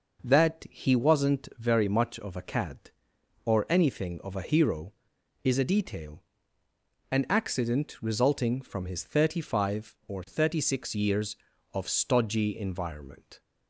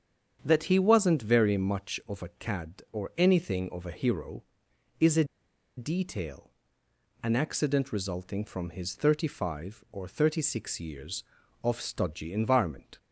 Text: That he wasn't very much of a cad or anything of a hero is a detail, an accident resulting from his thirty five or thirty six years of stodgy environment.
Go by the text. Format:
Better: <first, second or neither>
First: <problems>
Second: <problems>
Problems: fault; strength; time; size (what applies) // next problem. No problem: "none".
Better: first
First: none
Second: starts louder than the rest; strong; until 1.4 s; 8 dB // pauses between "a" and "detail"; noticeable; at 5.2 s; 0.53 s long